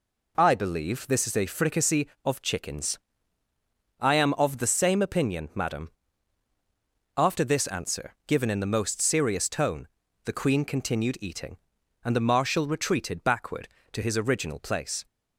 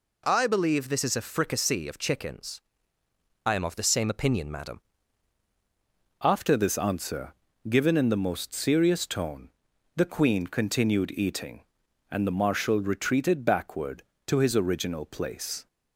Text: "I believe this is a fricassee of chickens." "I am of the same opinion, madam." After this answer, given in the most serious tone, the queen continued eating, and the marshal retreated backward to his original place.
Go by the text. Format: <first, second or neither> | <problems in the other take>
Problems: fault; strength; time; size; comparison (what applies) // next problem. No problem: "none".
first | changes voice at "After"; from 6.2 s on; 9.4 s long